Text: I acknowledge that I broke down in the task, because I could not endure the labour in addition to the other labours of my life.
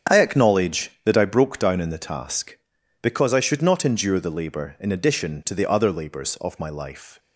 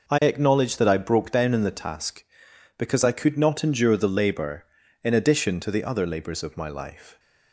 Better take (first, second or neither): second